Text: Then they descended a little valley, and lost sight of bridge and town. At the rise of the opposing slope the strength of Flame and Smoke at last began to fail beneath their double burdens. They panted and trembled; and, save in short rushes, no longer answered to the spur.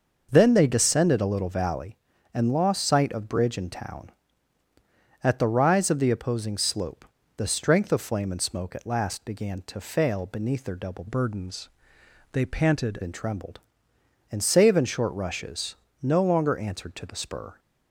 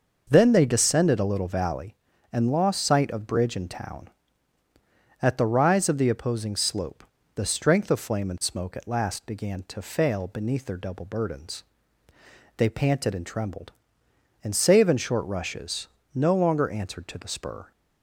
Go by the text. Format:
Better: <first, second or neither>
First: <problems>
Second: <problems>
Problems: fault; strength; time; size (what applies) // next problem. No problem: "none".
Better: second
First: pauses between "slope" and "the"; slight; at 7.0 s; 0.30 s long // changes voice from "burdens" to "panted"; from 11.0 to 12.9 s; 1.9 s long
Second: pauses between "slope" and "the"; slight; at 7.0 s; 0.30 s long